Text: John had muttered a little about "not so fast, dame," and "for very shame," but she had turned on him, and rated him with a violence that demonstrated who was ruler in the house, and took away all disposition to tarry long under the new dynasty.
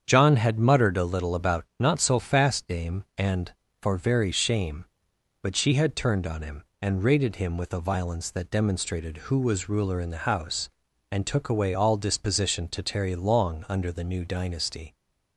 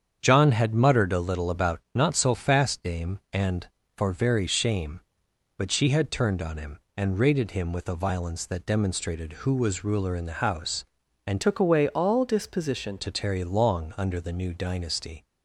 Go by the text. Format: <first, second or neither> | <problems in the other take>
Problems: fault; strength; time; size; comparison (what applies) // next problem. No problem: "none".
first | starts louder than the rest; strong; until 1.2 s; 8 dB; strong in the first // changes voice from "took" to "disposition"; from 11.4 to 12.9 s; 1.5 s long